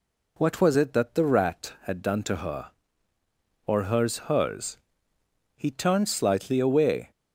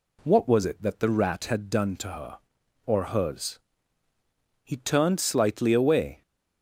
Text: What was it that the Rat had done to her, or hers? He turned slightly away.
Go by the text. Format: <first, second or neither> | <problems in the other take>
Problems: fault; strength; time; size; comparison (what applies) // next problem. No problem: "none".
second | says "hers" twice; at 4.2 s